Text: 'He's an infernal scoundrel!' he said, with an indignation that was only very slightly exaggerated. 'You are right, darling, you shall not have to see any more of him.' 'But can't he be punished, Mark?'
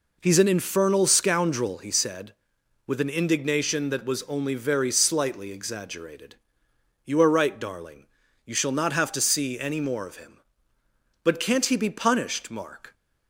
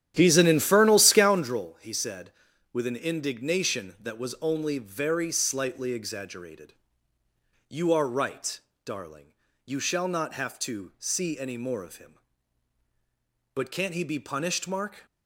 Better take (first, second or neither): first